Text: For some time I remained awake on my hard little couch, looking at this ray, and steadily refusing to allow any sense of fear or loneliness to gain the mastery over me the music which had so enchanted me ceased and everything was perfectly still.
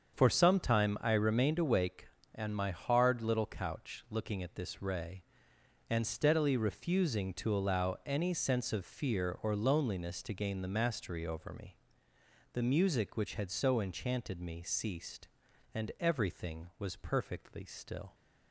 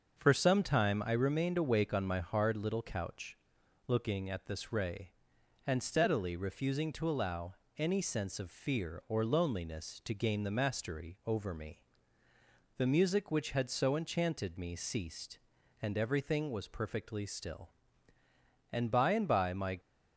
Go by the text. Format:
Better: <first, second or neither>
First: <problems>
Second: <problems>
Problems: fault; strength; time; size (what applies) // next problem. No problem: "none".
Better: first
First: starts louder than the rest; strong; until 1.1 s; 7 dB // pauses between "me" and "the"; noticeable; at 11.7 s; 0.78 s long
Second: starts louder than the rest; until 1.2 s; 6.5 dB // pauses between "allow" and "any"; slight; at 7.5 s; 0.24 s long // pauses between "me" and "the"; noticeable; at 11.8 s; 0.94 s long // goes on to say "And by and by my"; noticeable; from 18.7 s on; 1.0 s long